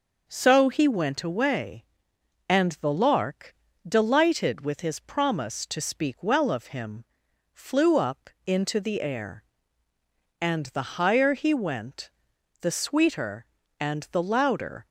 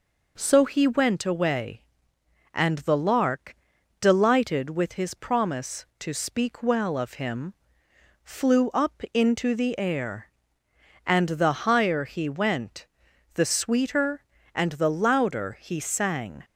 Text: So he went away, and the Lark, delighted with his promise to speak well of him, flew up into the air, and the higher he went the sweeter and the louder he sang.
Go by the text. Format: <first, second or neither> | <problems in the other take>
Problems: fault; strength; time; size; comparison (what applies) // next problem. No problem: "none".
second | pauses between "up" and "into"; slight; at 8.2 s; 0.16 s long // pauses between "went" and "the"; noticeable; at 12.0 s; 0.50 s long; noticeable in the second // stops before "he sang"; at 14.8 s